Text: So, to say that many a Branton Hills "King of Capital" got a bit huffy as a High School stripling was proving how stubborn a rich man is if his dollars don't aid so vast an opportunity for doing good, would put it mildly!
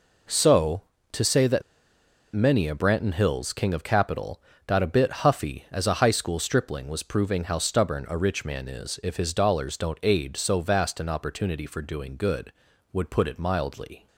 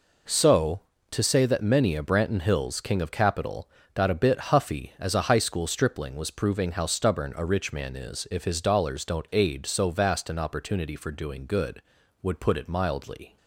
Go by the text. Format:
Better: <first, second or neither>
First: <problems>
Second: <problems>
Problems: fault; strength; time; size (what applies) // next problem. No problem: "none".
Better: second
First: pauses between "that" and "many"; noticeable; at 1.6 s; 0.72 s long // pauses between "Capital" and "got"; slight; at 4.4 s; 0.26 s long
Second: pauses between "Capital" and "got"; slight; at 3.6 s; 0.26 s long